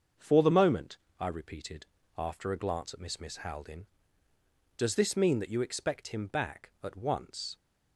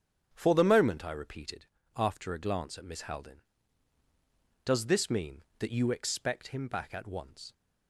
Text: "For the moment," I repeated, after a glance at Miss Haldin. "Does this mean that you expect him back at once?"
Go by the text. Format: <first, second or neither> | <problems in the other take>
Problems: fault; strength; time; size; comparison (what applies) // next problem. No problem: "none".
second | starts louder than the rest; until 1.4 s; 6.5 dB; strong in the second // says "Miss" twice; at 3.1 s